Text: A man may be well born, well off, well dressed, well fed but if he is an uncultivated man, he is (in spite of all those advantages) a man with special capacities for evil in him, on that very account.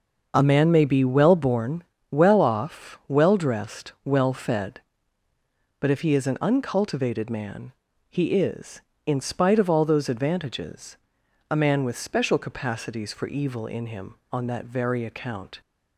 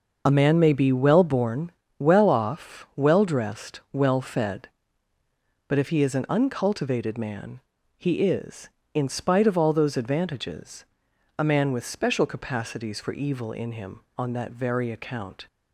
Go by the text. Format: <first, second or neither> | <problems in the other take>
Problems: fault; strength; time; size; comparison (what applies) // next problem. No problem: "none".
first | loses the start of "A"; at 0.2 s; 30 ms // starts louder than the rest; noticeable; until 1.2 s; 6 dB; also in the first